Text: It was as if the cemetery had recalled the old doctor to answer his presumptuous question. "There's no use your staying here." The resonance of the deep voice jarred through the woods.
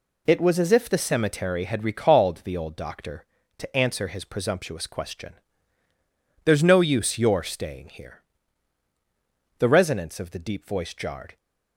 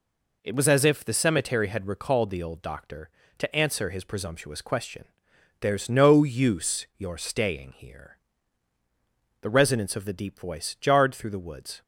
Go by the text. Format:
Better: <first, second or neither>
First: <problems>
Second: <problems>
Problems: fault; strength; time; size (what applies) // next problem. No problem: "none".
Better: second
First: stops before "through the woods"; at 11.3 s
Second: none